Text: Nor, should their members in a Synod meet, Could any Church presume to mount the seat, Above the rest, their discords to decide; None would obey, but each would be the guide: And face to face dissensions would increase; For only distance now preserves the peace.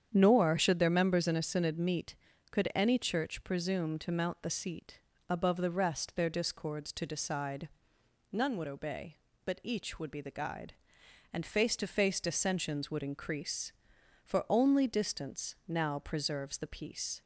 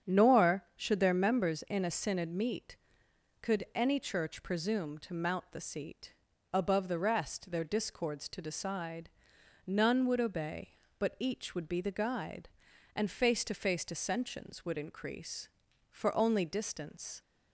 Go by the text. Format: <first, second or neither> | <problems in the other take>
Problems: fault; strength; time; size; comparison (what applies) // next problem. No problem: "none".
first | starts louder than the rest; strong; until 1.1 s; 8 dB; strong in the first // stops before "now preserves the peace"; at 17.2 s